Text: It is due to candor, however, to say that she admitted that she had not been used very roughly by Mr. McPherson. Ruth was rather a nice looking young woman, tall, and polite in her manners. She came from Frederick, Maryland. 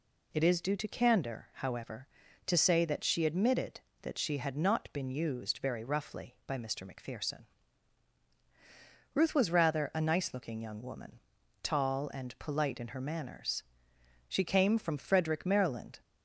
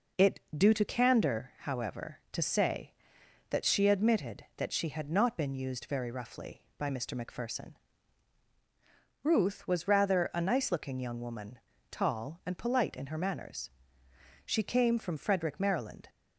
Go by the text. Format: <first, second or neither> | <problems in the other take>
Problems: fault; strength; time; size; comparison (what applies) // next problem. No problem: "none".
first | skips "is"; at 0.4 s